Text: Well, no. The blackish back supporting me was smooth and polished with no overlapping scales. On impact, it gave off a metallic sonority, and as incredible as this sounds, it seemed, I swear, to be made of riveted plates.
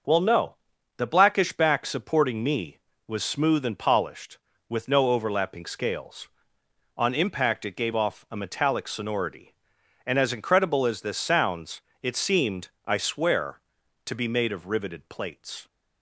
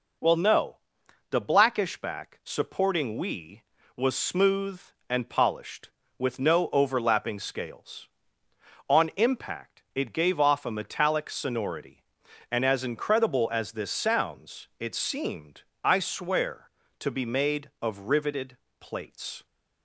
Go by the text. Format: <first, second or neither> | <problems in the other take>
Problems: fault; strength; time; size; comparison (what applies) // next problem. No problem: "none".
first | says "we" for "me"; at 3.1 s // pauses between "riveted" and "plates"; slight; at 18.5 s; 0.24 s long